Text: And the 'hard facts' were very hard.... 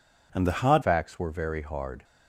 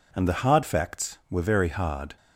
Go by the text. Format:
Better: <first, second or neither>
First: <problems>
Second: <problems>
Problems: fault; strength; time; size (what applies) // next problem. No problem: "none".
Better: second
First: changes voice at "facts"; from 0.8 s on; 1.2 s long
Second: none